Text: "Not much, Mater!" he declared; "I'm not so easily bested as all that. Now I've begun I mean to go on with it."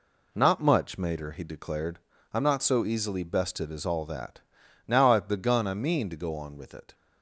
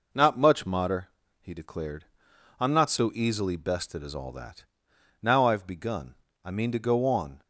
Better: first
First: none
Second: pauses between "begun" and "I"; slight; at 6.1 s; 0.28 s long // stops before "with it"; at 7.4 s

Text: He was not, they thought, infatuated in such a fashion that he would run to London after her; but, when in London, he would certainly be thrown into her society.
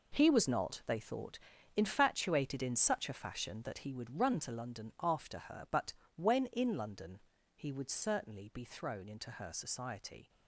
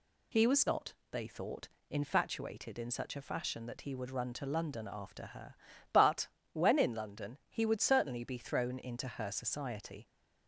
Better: second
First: gets quieter; strong; throughout; 10.5 dB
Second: none

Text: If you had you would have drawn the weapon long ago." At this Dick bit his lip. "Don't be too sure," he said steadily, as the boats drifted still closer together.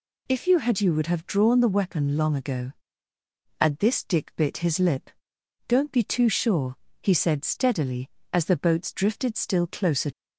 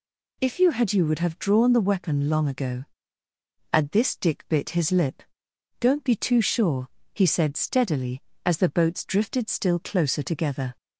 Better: second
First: stops before "together"; at 10.1 s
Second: none

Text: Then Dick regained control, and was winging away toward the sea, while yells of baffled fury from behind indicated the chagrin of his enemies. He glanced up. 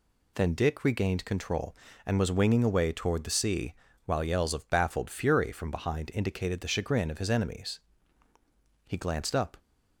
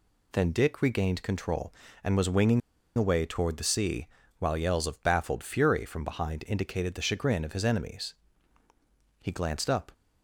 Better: first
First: none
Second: pauses between "winging" and "away"; at 2.6 s; 0.36 s long

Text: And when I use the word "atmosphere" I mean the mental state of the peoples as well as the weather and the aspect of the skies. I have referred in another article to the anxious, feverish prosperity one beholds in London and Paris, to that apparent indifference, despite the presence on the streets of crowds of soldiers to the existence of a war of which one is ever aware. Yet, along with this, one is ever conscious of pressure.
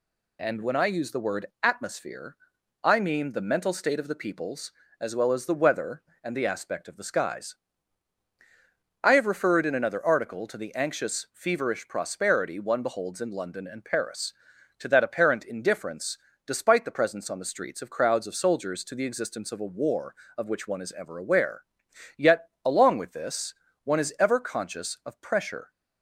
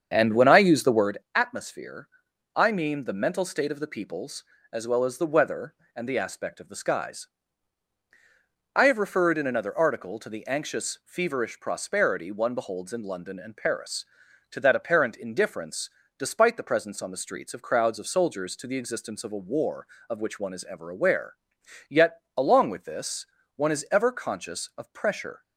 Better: first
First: pauses between "word" and "atmosphere"; slight; at 1.4 s; 0.18 s long // pauses between "atmosphere" and "I"; noticeable; at 2.3 s; 0.48 s long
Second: starts louder than the rest; strong; until 1.1 s; 7.5 dB // pauses between "word" and "atmosphere"; slight; at 1.1 s; 0.18 s long // pauses between "atmosphere" and "I"; noticeable; at 2.0 s; 0.48 s long

